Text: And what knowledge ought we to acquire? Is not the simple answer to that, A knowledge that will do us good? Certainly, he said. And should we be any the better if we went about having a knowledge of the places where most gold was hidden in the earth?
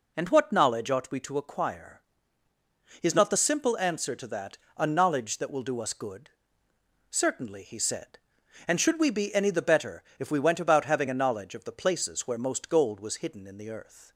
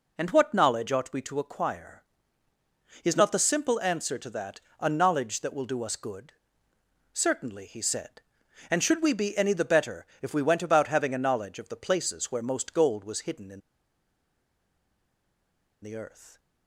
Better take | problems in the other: first | pauses between "better" and "if"; slight; at 10.0 s; 0.16 s long; slight in the first // pauses between "in" and "the"; strong; at 13.6 s; 2.2 s long

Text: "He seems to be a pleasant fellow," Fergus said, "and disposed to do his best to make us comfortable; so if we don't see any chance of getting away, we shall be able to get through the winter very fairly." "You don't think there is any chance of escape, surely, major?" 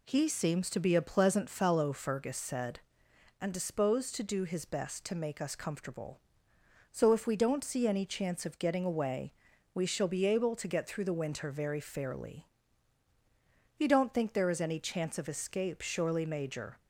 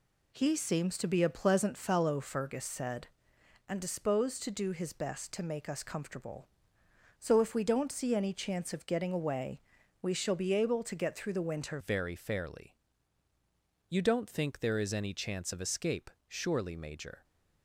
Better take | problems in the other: first | changes voice at "very"; from 11.8 s on; 5.4 s long

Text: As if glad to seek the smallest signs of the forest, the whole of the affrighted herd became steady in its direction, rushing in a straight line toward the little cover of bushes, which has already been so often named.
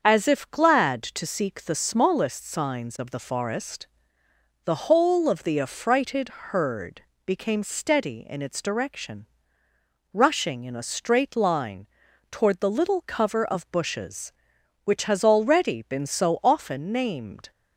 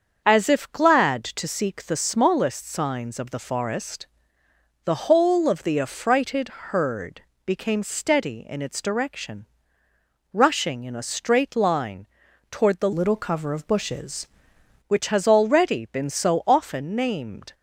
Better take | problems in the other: first | starts louder than the rest; until 1.2 s; 7 dB; also in the first // pauses between "herd" and "became"; slight; at 7.2 s; 0.24 s long; slight in the first // pauses between "line" and "toward"; at 12.0 s; 0.44 s long; also in the first // changes voice from "little" to "bushes"; from 12.9 to 14.2 s; 1.3 s long

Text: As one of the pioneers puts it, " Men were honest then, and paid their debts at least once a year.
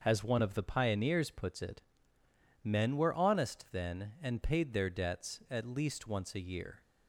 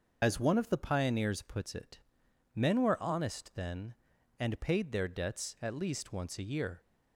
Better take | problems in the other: first | loses the start of "As"; at 0.2 s; 65 ms // starts louder than the rest; until 1.2 s; 6.5 dB; also in the first

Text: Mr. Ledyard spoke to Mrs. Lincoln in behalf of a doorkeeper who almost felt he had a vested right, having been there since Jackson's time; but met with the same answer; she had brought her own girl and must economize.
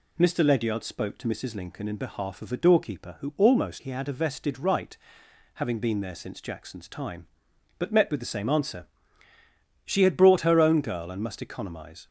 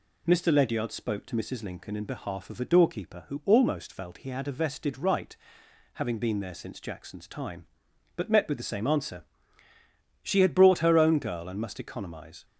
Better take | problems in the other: second | skips "felt"; at 3.8 s

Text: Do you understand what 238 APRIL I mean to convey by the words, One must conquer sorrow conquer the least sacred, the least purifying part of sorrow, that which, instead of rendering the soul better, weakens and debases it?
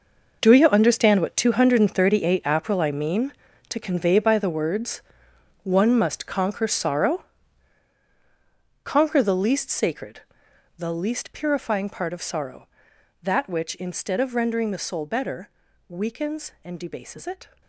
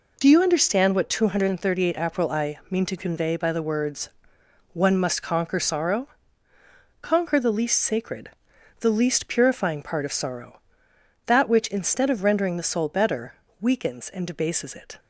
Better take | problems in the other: second | gets quieter; strong; throughout; 13 dB // pauses between "sorrow" and "conquer"; strong; at 7.2 s; 1.6 s long; noticeable in the second

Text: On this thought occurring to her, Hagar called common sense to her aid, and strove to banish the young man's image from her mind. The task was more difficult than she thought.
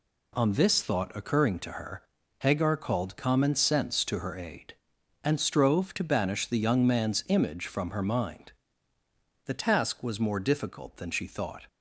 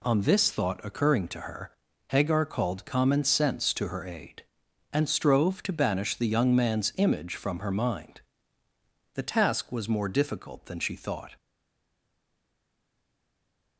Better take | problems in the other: first | stays silent after the last word; from 11.3 s on; 2.4 s long

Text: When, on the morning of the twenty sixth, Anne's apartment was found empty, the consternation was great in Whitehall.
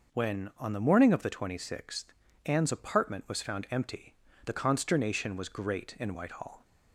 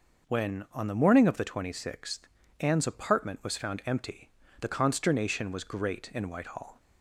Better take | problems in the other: neither | none

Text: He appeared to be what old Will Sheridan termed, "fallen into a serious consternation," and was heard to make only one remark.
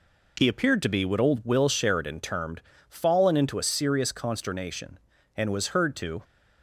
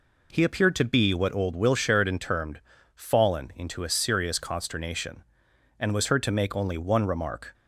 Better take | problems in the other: second | stops before "make only one remark"; at 6.2 s

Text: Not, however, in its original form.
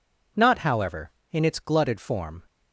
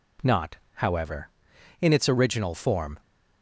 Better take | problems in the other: second | says "glutted" for "original"; at 1.6 s

